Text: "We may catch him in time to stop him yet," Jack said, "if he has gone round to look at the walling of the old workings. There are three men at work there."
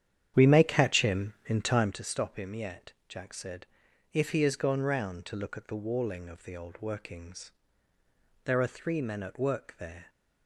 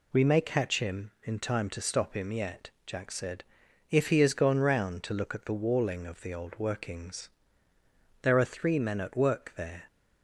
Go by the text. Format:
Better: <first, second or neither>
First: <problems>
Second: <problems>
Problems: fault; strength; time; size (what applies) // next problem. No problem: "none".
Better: second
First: starts louder than the rest; strong; until 2.0 s; 9.5 dB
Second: none